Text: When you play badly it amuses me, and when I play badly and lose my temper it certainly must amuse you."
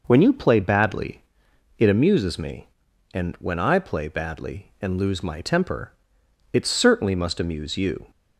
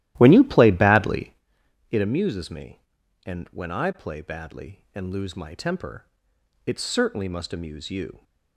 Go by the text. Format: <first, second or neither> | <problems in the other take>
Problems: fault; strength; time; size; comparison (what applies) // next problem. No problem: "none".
first | starts louder than the rest; strong; until 1.4 s; 14 dB // pauses between "badly" and "it"; noticeable; at 1.3 s; 0.56 s long; noticeable in the first // pauses between "temper" and "it"; noticeable; at 6.0 s; 0.58 s long; noticeable in the first